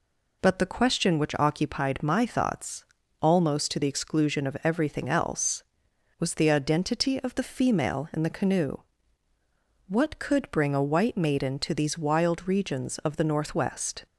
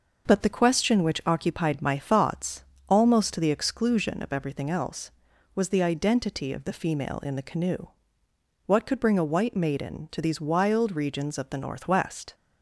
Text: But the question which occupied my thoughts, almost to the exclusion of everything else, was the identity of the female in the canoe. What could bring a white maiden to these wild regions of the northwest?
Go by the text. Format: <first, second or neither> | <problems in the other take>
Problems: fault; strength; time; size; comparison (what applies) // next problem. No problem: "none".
neither | none